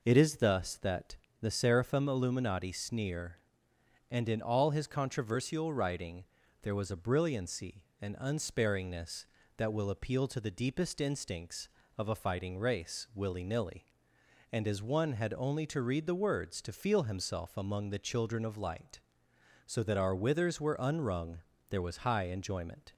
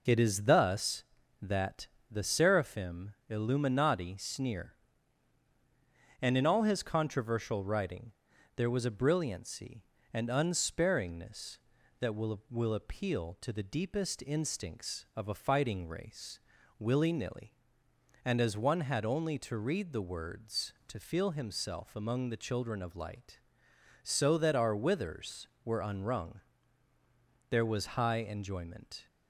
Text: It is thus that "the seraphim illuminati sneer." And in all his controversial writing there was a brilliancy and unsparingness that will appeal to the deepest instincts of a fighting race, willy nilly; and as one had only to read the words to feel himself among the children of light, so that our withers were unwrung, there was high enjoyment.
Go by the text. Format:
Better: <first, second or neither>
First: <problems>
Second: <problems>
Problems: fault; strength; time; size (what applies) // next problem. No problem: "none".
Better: first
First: pauses between "that" and "the"; slight; at 1.1 s; 0.26 s long // pauses between "writing" and "there"; at 6.2 s; 0.40 s long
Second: pauses between "that" and "the"; slight; at 1.8 s; 0.20 s long // pauses between "writing" and "there"; at 8.1 s; 0.42 s long // says "will" twice; at 12.4 s